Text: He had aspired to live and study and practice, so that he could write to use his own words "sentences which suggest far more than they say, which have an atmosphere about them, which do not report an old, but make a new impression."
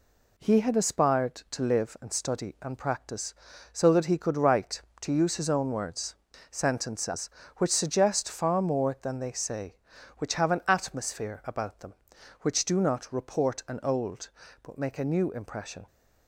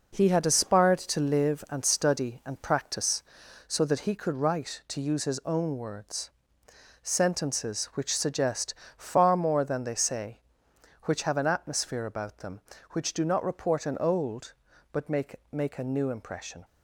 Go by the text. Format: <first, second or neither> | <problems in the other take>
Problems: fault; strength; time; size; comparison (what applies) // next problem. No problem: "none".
first | pauses between "words" and "sentences"; noticeable; at 6.2 s; 0.72 s long; slight in the first // pauses between "suggest" and "far"; slight; at 8.7 s; 0.20 s long // says "make" twice; at 15.5 s